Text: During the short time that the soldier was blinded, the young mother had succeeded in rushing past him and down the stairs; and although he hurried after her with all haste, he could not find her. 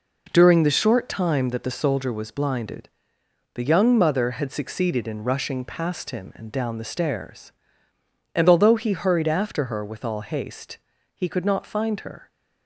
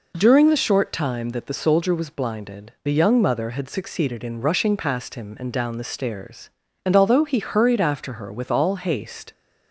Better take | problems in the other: first | stops before "he could not find her"; at 9.3 s

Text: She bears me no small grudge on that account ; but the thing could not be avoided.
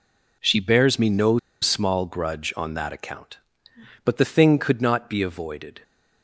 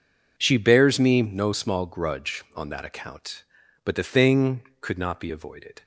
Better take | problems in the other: second | pauses between "no" and "small"; slight; at 1.3 s; 0.23 s long

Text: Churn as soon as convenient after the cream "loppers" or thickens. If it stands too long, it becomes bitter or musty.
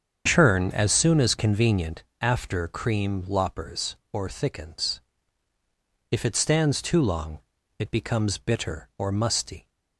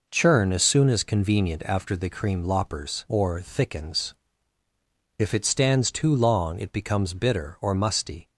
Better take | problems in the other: second | starts louder than the rest; strong; until 1.2 s; 7 dB // pauses between "convenient" and "after"; slight; at 2.0 s; 0.18 s long // skips "the"; at 2.6 s

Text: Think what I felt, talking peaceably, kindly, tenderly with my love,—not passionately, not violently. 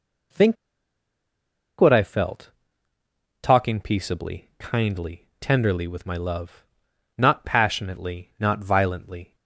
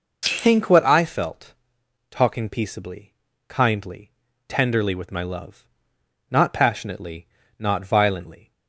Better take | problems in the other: second | pauses between "Think" and "what"; at 0.5 s; 1.2 s long

